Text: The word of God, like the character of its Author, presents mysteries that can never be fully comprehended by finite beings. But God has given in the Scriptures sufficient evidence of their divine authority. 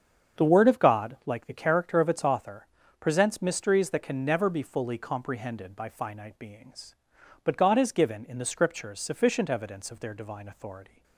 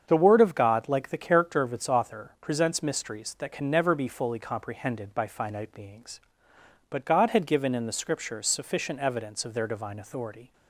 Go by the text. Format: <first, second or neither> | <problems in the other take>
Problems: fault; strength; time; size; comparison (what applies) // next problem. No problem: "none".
first | starts louder than the rest; strong; until 1.0 s; 7.5 dB; strong in the first // says "had" for "has"; at 7.3 s